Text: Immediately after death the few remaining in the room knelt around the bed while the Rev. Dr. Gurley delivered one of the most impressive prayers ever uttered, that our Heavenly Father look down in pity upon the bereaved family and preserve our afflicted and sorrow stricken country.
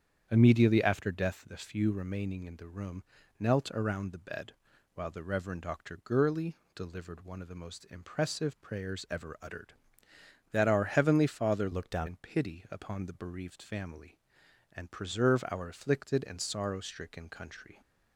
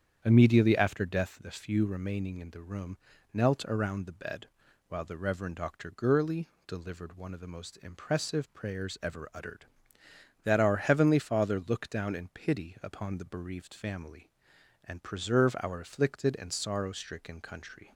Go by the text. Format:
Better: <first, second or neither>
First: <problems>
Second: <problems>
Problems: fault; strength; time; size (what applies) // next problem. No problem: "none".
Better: second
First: starts louder than the rest; strong; until 1.3 s; 8.5 dB // pauses between "room" and "knelt"; slight; at 3.0 s; 0.36 s long // pauses between "bed" and "while"; at 4.5 s; 0.42 s long // pauses between "Gurley" and "delivered"; slight; at 6.5 s; 0.18 s long // changes voice from "look" to "down"; from 11.7 to 12.0 s; 0.3 s long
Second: starts louder than the rest; strong; until 1.2 s; 8.5 dB // pauses between "room" and "knelt"; slight; at 2.9 s; 0.36 s long // pauses between "bed" and "while"; at 4.4 s; 0.42 s long // pauses between "Gurley" and "delivered"; slight; at 6.4 s; 0.18 s long